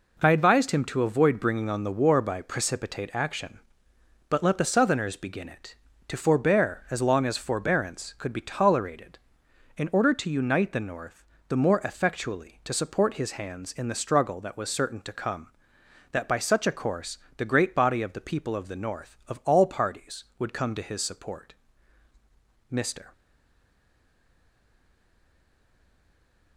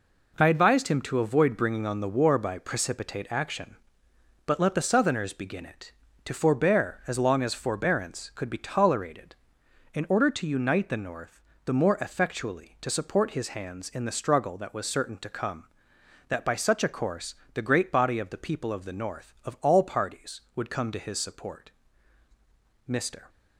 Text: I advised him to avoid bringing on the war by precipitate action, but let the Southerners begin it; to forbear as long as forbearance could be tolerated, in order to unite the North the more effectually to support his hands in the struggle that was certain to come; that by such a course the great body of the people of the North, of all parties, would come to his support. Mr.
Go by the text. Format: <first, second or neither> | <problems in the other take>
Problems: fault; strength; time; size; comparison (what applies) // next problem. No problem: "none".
second | pauses between "North" and "the"; slight; at 11.2 s; 0.26 s long; slight in the second // pauses between "course" and "the"; slight; at 17.1 s; 0.18 s long; slight in the second // stays silent after the last word; strong; from 23.1 s on; 3.4 s long